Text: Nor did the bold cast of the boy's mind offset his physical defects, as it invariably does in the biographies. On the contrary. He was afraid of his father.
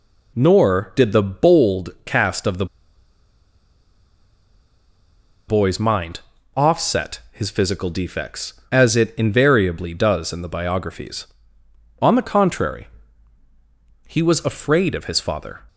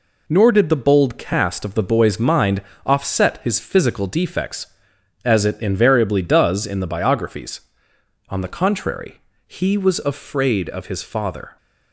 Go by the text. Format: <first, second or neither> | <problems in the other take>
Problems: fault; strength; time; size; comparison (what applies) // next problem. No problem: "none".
second | pauses between "bold" and "cast"; slight; at 1.8 s; 0.16 s long // pauses between "the" and "boy's"; strong; at 2.6 s; 2.8 s long // pauses between "mind" and "offset"; slight; at 6.2 s; 0.34 s long; slight in the second